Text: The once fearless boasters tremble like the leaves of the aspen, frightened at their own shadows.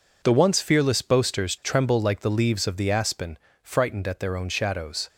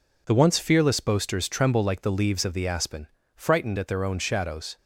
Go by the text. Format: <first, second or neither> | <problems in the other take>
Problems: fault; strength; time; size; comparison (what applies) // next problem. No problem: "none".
second | gets quieter; strong; throughout; 10 dB